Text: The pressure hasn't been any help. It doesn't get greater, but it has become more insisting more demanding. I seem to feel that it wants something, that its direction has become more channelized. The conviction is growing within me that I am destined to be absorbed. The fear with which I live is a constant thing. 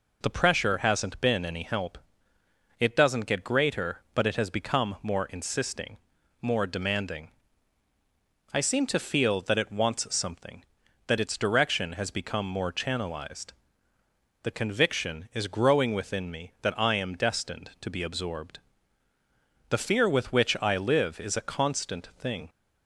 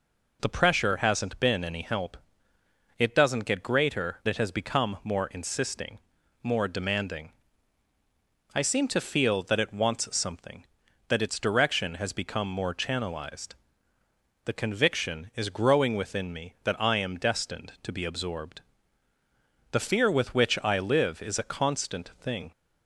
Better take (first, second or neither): first